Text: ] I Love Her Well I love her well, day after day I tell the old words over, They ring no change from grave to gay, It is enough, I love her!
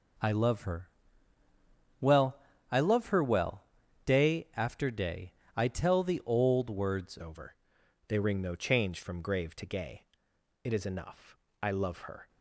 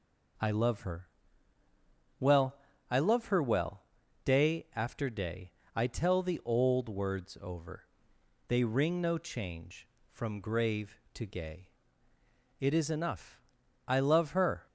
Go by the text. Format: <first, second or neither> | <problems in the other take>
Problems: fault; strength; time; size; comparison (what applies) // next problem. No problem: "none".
second | pauses between "Her" and "Well"; at 0.8 s; 1.1 s long; also in the second // pauses between "Well" and "I"; slight; at 2.3 s; 0.36 s long; slight in the second // pauses between "day" and "I"; slight; at 5.3 s; 0.24 s long; slight in the second // changes voice at "over"; from 7.1 s on; 5.1 s long